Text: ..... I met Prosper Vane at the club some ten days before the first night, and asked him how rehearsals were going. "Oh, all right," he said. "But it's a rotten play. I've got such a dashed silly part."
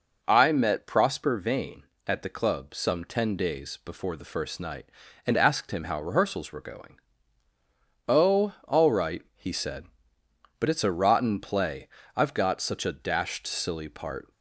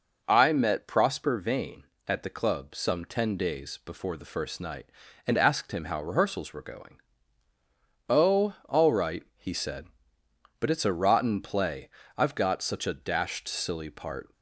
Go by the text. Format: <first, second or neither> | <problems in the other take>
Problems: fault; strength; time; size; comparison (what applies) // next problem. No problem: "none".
neither | none